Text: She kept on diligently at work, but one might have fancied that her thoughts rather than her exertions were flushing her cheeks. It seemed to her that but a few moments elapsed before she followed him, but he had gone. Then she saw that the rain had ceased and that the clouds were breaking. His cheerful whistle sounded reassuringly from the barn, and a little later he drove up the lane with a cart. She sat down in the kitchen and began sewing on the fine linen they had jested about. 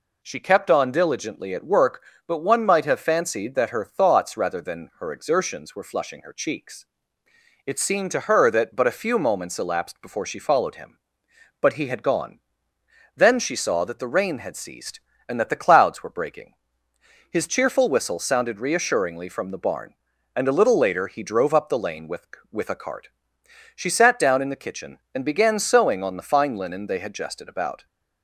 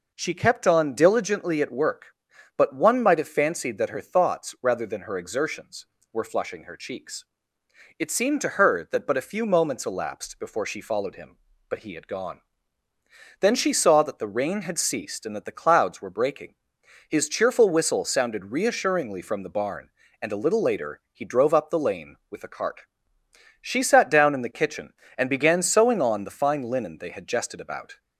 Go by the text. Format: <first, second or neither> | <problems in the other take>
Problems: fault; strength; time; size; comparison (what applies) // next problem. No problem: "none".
second | says "with" twice; at 22.5 s